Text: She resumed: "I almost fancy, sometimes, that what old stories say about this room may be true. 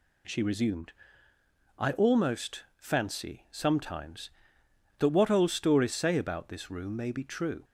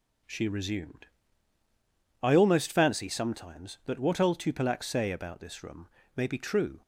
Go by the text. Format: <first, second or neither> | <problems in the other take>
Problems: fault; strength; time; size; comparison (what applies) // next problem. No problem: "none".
first | says "tupilak" for "stories"; at 4.3 s // pauses between "room" and "may"; slight; at 5.8 s; 0.26 s long